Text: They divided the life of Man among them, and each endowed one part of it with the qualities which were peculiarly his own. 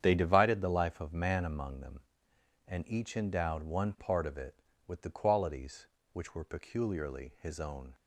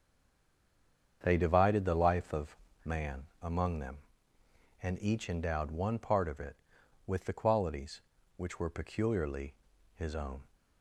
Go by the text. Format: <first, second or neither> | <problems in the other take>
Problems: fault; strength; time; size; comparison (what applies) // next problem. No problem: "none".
first | stays silent before the first word; noticeable; until 1.2 s; 1.2 s long // starts louder than the rest; strong; until 2.2 s; 7.5 dB; strong in the first // pauses between "of" and "Man"; slight; at 2.5 s; 0.28 s long // pauses between "Man" and "among"; slight; at 3.2 s; 0.22 s long // pauses between "peculiarly" and "his"; at 9.5 s; 0.41 s long